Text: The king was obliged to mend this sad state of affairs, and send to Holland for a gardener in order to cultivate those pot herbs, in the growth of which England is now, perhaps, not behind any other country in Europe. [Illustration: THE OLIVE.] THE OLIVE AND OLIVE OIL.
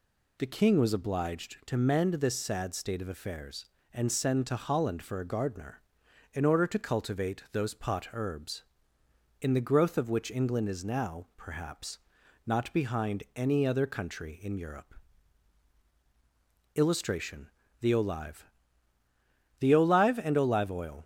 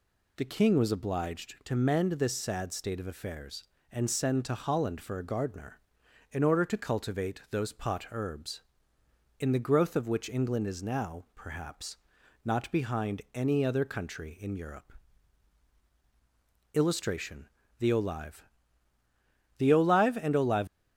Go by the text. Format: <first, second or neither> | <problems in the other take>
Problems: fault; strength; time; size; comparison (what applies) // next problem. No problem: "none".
first | stops before "OIL"; at 20.6 s